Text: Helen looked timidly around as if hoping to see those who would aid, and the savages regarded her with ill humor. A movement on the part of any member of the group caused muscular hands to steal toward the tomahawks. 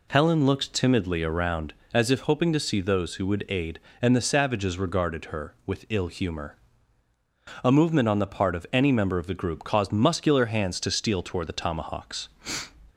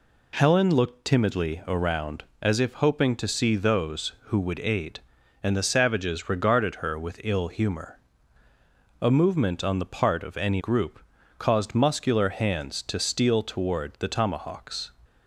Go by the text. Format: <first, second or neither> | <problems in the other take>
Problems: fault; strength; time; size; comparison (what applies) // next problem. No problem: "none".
first | skips "member of the"; at 10.5 s // pauses between "group" and "caused"; at 10.9 s; 0.38 s long